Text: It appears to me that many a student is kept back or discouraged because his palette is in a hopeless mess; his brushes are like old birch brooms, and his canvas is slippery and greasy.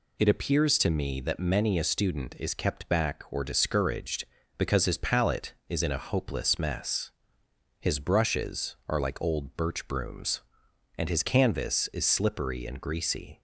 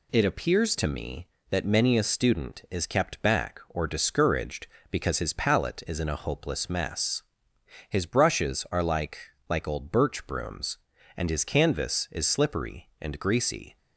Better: first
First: none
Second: says "like" twice; at 9.4 s

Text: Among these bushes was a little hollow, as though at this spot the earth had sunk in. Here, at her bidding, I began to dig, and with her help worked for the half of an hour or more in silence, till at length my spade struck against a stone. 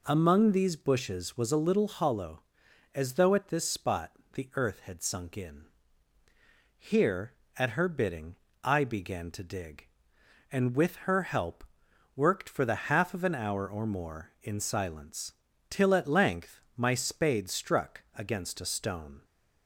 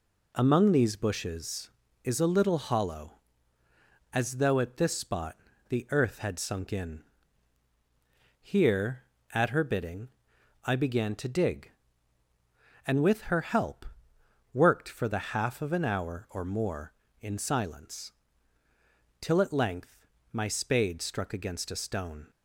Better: first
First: pauses between "spot" and "the"; slight; at 4.0 s; 0.24 s long // pauses between "help" and "worked"; noticeable; at 11.6 s; 0.52 s long // pauses between "length" and "my"; slight; at 16.5 s; 0.16 s long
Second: says "is" for "was"; at 2.0 s // pauses between "spot" and "the"; slight; at 5.3 s; 0.36 s long // pauses between "help" and "worked"; noticeable; at 13.8 s; 0.70 s long // pauses between "length" and "my"; slight; at 20.0 s; 0.26 s long

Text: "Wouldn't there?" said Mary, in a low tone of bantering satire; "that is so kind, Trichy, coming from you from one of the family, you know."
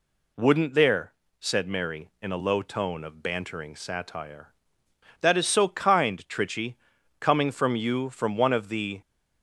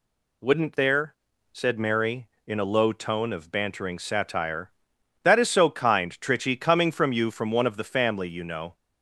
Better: second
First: stops before "family you know"; at 9.0 s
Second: none

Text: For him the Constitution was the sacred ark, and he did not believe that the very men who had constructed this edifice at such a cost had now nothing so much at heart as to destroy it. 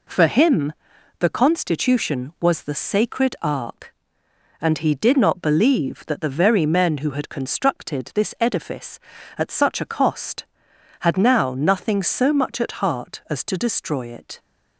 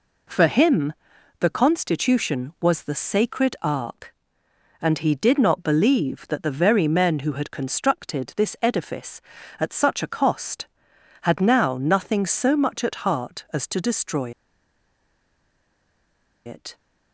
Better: first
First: pauses between "him" and "the"; noticeable; at 0.7 s; 0.48 s long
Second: pauses between "him" and "the"; noticeable; at 0.9 s; 0.48 s long // pauses between "destroy" and "it"; strong; at 14.3 s; 2.1 s long

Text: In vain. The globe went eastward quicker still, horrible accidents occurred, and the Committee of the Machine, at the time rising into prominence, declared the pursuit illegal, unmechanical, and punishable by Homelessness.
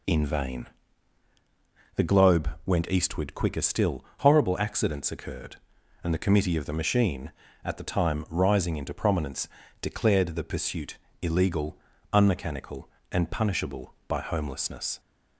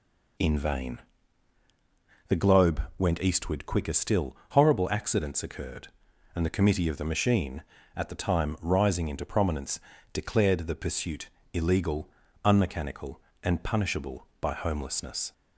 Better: neither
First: pauses between "globe" and "went"; slight; at 2.4 s; 0.16 s long // pauses between "pursuit" and "illegal"; slight; at 10.9 s; 0.26 s long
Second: pauses between "globe" and "went"; slight; at 2.8 s; 0.16 s long // pauses between "pursuit" and "illegal"; slight; at 11.2 s; 0.26 s long

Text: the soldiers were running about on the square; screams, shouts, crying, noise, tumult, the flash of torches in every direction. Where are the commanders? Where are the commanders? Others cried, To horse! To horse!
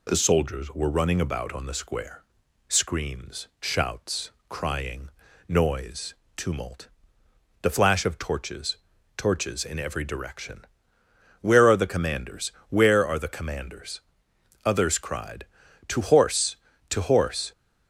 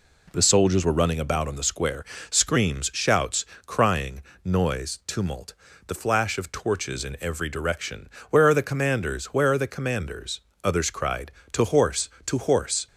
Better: second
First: says "torches" twice; at 9.1 s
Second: none

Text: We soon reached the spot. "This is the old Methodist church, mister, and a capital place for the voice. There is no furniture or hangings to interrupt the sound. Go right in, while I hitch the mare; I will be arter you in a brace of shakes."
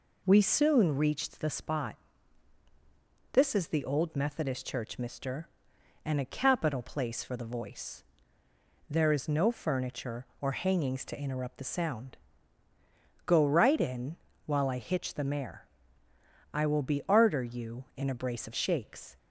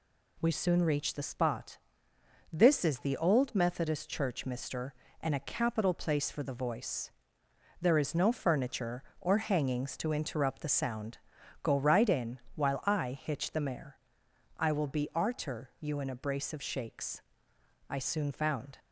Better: first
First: none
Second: goes on to say "I soon found"; noticeable; from 17.8 s on; 0.90 s long

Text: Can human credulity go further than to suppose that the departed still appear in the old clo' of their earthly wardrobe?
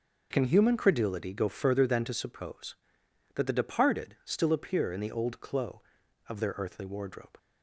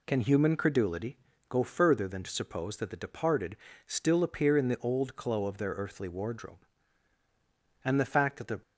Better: first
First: none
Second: pauses between "credulity" and "go"; slight; at 1.1 s; 0.32 s long // pauses between "departed" and "still"; slight; at 3.5 s; 0.30 s long // goes on to say "and the fact that the"; noticeable; from 7.8 s on; 0.74 s long

